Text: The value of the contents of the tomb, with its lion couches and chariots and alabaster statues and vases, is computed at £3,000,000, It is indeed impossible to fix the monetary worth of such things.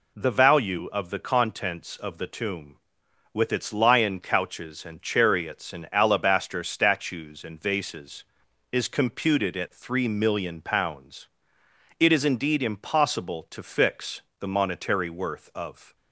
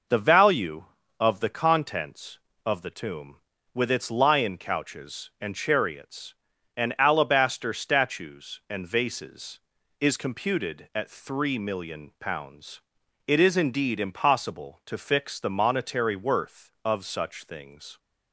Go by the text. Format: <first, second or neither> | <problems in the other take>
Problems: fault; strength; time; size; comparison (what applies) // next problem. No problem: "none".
second | pauses between "fix" and "the"; slight; at 14.2 s; 0.18 s long // stops before "such things"; at 15.9 s